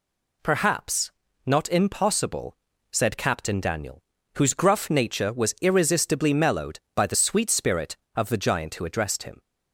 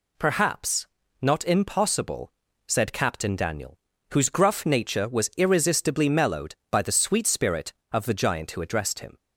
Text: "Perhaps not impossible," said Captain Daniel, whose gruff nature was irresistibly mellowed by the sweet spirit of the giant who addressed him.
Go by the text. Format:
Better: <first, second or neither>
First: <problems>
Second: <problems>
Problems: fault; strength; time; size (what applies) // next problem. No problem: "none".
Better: neither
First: pauses between "Perhaps" and "not"; slight; at 1.1 s; 0.34 s long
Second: pauses between "Perhaps" and "not"; slight; at 0.8 s; 0.34 s long